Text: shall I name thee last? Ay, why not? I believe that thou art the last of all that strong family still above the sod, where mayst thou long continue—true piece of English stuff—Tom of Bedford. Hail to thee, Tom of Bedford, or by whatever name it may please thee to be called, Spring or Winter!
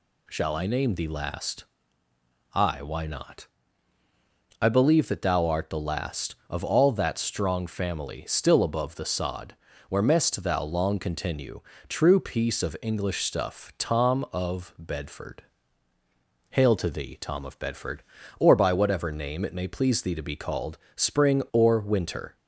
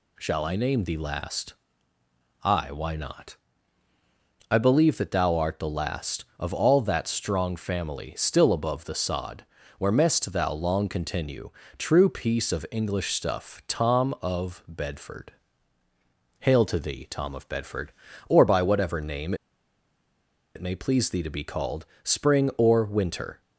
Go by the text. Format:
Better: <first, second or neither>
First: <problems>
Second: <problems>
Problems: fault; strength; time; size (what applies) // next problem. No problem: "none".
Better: first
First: none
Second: pauses between "name" and "it"; at 19.3 s; 1.2 s long